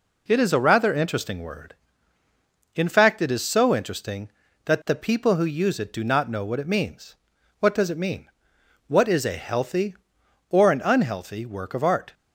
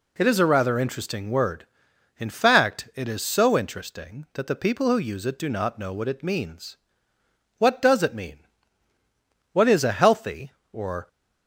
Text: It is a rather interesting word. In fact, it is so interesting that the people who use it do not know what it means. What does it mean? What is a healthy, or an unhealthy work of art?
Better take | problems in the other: first | stops before "an unhealthy work of art"; at 11.0 s

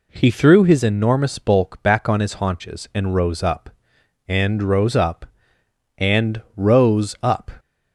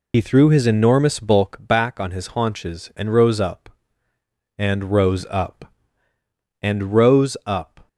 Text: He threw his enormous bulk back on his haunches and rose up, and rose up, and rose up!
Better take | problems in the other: first | loses the start of "He"; at 0.1 s; 60 ms

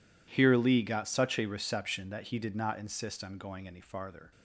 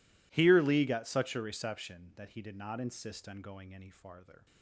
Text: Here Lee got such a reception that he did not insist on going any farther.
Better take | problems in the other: neither | none

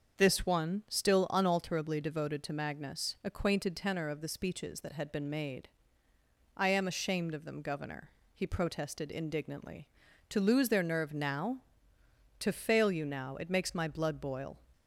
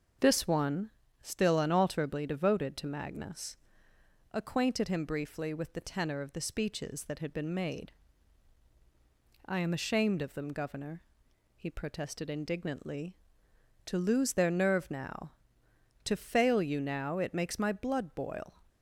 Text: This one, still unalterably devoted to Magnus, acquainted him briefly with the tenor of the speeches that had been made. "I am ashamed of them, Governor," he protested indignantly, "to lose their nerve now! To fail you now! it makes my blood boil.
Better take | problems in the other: second | starts louder than the rest; until 1.2 s; 6.5 dB; also in the second // skips "him briefly with the"; at 3.7 s

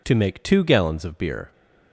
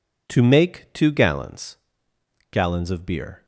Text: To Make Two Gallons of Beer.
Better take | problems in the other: first | says "Gallons" twice; at 2.5 s

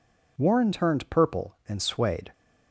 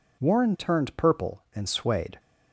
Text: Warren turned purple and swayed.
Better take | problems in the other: neither | none

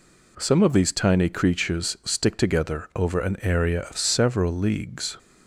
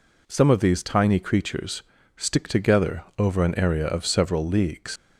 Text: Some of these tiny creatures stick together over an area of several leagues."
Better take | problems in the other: first | pauses between "creatures" and "stick"; slight; at 1.8 s; 0.34 s long // pauses between "together" and "over"; slight; at 3.0 s; 0.16 s long // leaves "leagues" unfinished; at 4.9 s; 100 ms

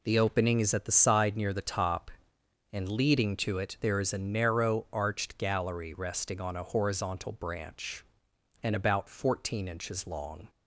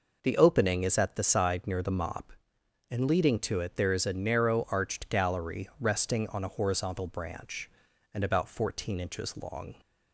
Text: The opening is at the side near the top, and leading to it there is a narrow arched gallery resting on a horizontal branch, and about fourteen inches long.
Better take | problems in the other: first | says "mop" for "top"; at 1.8 s

